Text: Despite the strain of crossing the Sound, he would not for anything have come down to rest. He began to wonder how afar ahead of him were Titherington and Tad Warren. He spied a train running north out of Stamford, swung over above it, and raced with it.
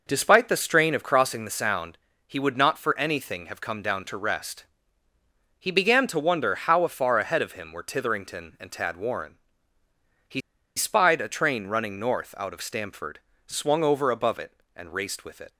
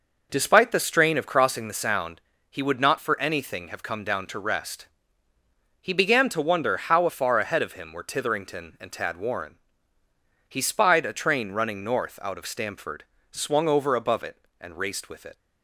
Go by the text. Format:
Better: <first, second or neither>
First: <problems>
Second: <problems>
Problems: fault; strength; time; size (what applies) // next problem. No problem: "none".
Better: second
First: pauses between "He" and "spied"; at 10.3 s; 0.36 s long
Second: none